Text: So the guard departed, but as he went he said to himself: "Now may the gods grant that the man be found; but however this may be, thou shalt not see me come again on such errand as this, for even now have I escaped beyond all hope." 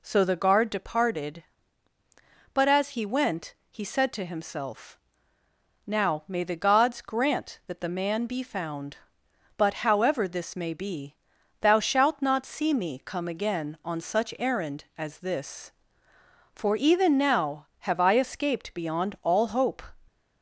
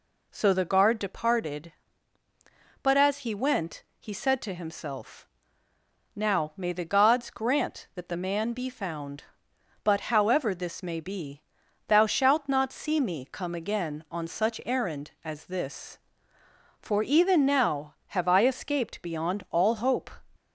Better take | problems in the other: neither | pauses between "went" and "he"; slight; the same in both

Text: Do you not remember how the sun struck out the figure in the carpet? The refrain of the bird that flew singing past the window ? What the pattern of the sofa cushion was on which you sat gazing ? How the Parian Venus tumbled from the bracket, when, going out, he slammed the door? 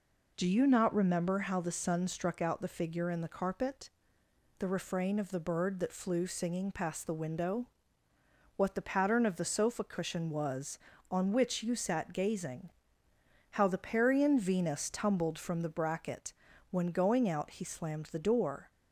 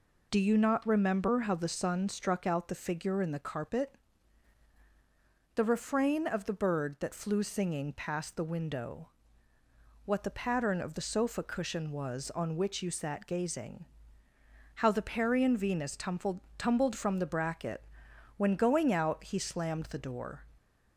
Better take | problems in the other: first | says "tumbled" twice; at 16.5 s

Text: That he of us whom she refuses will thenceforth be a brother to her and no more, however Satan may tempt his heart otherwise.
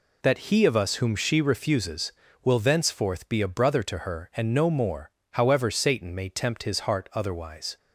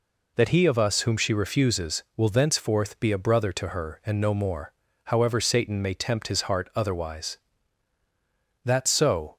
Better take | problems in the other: first | goes on to say "That so"; noticeable; from 8.6 s on; 0.72 s long

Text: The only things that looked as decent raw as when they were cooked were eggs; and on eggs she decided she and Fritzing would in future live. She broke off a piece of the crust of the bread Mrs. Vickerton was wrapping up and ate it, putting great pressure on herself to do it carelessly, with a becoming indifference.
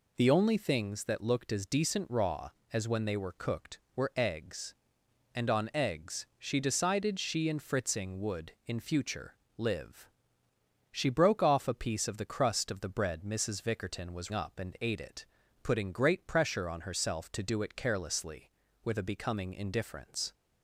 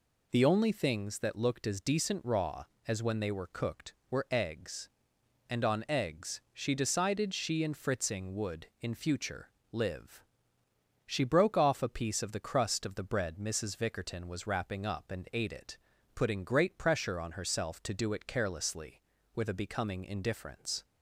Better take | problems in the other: second | pauses between "future" and "live"; slight; at 9.3 s; 0.20 s long; slight in the second // skips "wrapping"; at 14.3 s

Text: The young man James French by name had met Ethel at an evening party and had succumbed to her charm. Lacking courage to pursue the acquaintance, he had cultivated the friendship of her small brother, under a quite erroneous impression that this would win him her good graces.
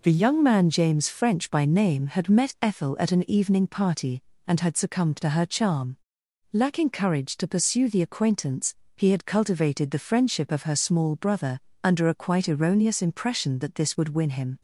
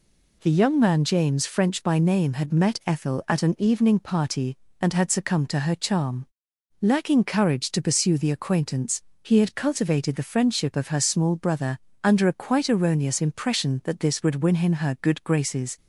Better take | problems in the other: second | stops before "her good graces"; at 14.5 s

